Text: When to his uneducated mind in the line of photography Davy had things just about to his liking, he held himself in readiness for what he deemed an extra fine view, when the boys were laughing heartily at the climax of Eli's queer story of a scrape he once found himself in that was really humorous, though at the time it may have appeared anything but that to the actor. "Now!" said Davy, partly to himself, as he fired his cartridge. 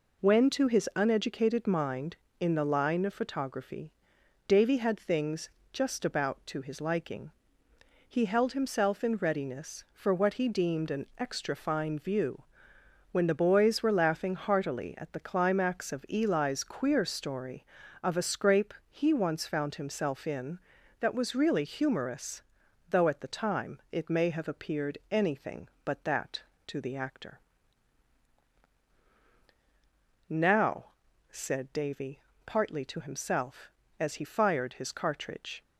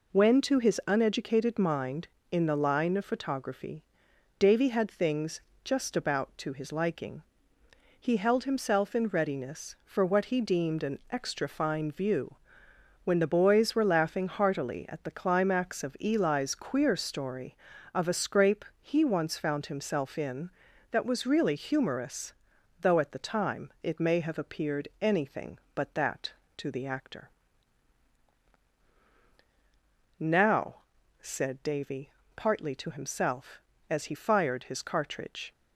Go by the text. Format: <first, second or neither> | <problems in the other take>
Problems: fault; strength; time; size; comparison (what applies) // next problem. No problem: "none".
neither | pauses between "photography" and "Davy"; noticeable; the same in both // pauses between "things" and "just"; slight; the same in both // pauses between "scrape" and "he"; slight; the same in both